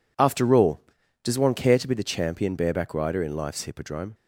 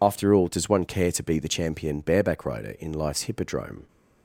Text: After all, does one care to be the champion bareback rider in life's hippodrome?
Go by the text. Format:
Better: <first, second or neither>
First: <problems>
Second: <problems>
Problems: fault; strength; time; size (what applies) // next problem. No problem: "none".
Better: first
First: none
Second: loses the start of "After"; at 0.0 s; 25 ms